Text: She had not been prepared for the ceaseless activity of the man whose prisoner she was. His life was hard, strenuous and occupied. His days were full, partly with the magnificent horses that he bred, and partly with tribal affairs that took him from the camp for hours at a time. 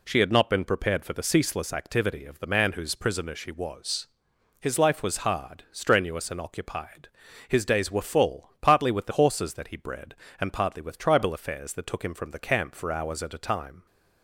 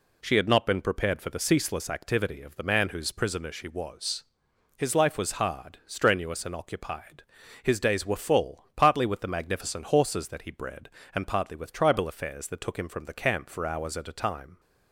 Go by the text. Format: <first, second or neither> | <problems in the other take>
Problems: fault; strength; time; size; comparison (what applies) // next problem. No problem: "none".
second | skips "magnificent"; at 9.1 s